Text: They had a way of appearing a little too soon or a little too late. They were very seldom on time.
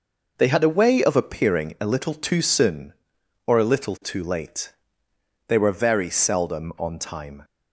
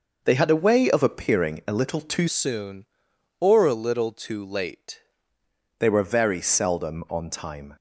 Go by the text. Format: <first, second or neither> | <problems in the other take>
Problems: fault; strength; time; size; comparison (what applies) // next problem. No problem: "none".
first | changes voice from "soon" to "late"; from 2.2 to 5.0 s; 2.8 s long